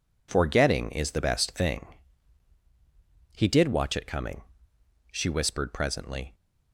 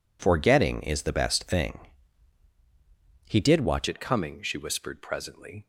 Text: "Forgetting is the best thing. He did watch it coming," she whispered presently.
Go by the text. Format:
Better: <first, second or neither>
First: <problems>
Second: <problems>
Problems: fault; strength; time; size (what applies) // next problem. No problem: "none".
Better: first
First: none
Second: changes voice at "it"; from 3.8 s on; 1.8 s long